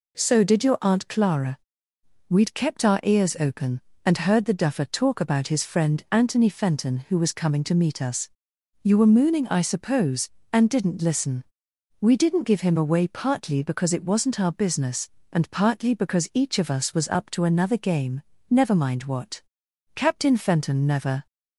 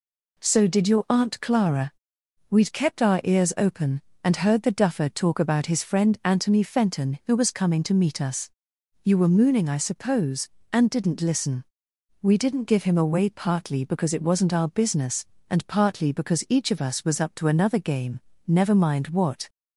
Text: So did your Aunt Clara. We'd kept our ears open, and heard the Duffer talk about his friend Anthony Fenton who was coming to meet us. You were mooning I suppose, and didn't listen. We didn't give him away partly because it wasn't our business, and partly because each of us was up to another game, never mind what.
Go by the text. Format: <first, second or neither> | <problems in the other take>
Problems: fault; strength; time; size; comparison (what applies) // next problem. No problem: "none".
second | goes on to say "Captain Fenton never"; noticeable; from 19.9 s on; 1.3 s long